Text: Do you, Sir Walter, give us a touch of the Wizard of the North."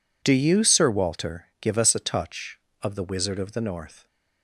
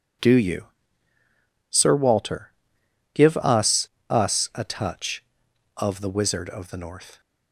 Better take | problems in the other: first | says "us" twice; at 4.1 s

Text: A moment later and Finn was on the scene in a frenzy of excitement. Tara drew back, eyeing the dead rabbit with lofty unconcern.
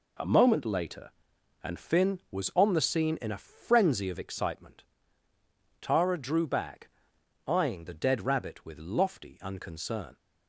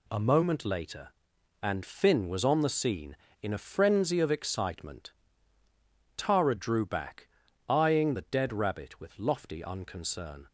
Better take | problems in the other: neither | none

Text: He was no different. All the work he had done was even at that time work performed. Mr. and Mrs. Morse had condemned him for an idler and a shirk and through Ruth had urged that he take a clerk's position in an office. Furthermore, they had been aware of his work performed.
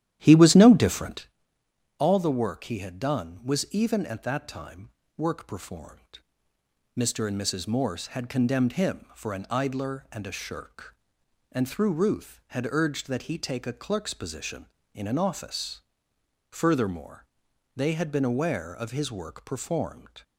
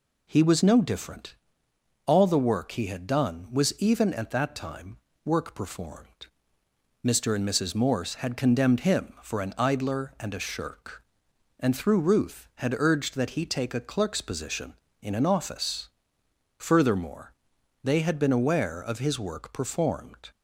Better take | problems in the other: second | starts louder than the rest; strong; until 1.3 s; 11.5 dB // pauses between "time" and "work"; slight; at 4.8 s; 0.26 s long; slight in the second

